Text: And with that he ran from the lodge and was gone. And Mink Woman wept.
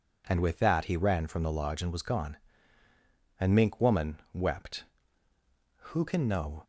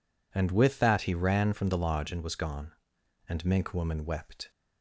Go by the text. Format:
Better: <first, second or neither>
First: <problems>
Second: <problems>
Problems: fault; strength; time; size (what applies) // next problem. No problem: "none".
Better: second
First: goes on to say "Who can know"; noticeable; from 5.9 s on; 0.72 s long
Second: none